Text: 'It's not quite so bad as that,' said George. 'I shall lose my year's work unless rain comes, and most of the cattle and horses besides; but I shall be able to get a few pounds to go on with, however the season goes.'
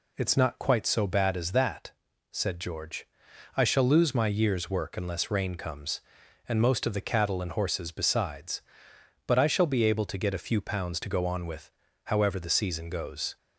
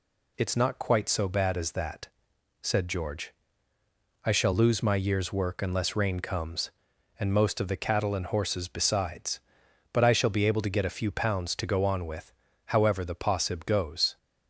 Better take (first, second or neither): first